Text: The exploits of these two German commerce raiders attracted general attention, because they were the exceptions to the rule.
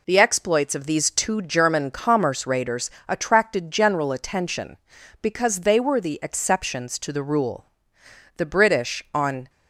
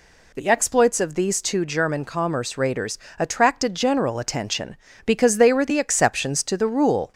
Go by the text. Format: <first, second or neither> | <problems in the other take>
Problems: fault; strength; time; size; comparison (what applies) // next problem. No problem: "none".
second | pauses between "raiders" and "attracted"; slight; at 2.9 s; 0.18 s long; slight in the second // goes on to say "The British on"; noticeable; from 8.3 s on; 1.1 s long